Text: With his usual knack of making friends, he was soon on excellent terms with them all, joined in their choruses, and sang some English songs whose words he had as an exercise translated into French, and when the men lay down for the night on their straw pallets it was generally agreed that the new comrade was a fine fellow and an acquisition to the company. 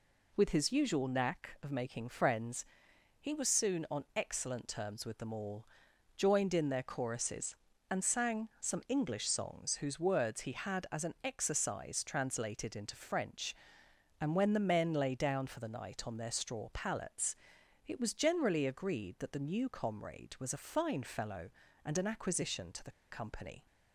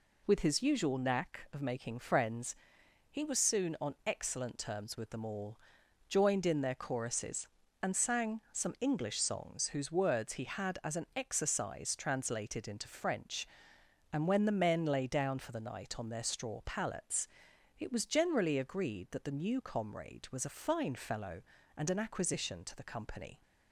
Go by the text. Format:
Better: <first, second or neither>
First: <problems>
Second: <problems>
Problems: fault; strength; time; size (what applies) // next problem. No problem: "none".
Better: second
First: pauses between "pallets" and "it"; noticeable; at 17.3 s; 0.50 s long // pauses between "the" and "company"; slight; at 22.9 s; 0.16 s long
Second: pauses between "pallets" and "it"; noticeable; at 17.2 s; 0.50 s long